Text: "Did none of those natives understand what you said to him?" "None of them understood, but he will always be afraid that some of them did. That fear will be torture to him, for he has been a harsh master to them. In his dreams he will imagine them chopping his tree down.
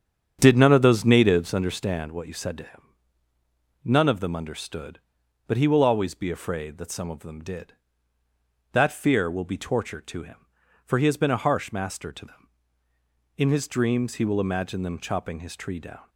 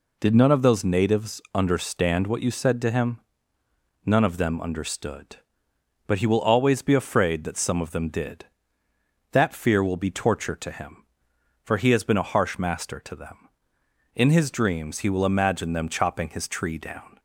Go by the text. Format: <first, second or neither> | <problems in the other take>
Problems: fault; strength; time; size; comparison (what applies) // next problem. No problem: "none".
second | starts louder than the rest; strong; until 1.5 s; 8.5 dB